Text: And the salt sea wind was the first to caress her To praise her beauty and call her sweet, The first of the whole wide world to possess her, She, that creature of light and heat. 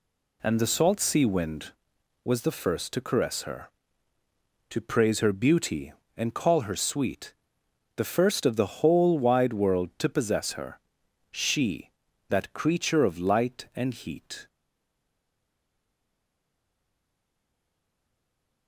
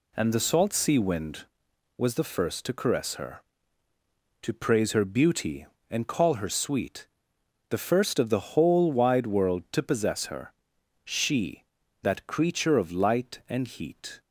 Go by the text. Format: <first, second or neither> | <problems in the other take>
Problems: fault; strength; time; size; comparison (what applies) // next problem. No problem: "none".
second | stays silent after the last word; strong; from 14.4 s on; 4.2 s long